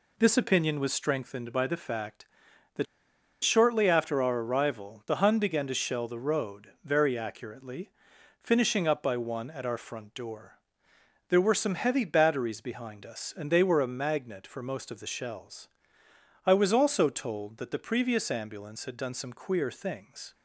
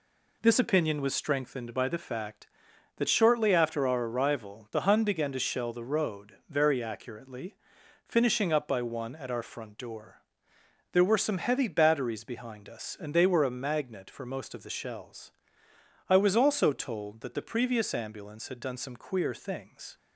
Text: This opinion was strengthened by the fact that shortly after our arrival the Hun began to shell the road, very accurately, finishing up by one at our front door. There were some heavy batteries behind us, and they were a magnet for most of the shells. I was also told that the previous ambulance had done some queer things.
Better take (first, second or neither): second